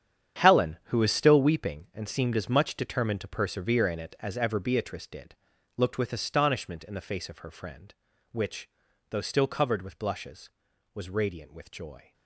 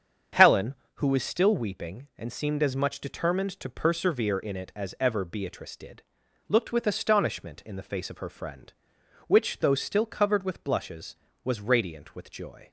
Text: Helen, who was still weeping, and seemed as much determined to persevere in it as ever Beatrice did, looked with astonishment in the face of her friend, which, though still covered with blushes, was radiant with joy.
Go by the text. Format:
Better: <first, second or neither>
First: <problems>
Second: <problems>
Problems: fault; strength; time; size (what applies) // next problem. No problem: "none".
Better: second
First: gets quieter; strong; throughout; 13.5 dB // starts louder than the rest; strong; until 1.4 s; 9 dB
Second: starts louder than the rest; strong; until 1.5 s; 7.5 dB